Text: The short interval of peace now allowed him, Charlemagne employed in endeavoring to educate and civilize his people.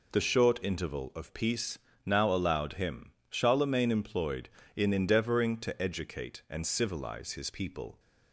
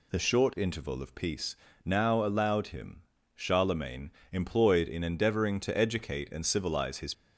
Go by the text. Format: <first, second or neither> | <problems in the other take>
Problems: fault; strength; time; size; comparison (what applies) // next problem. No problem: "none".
first | pauses between "peace" and "now"; slight; at 1.5 s; 0.30 s long; slight in the first // pauses between "Charlemagne" and "employed"; slight; at 4.0 s; 0.20 s long // stops before "people"; at 7.1 s